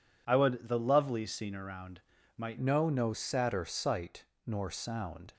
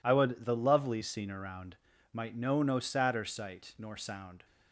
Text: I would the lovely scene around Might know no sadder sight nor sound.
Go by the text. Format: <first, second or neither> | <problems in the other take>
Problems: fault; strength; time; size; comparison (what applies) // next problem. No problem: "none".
second | pauses between "around" and "Might"; slight; at 2.0 s; 0.36 s long; slight in the second // changes voice at "know"; from 2.6 s on; 2.7 s long // pauses between "sight" and "nor"; slight; at 4.2 s; 0.18 s long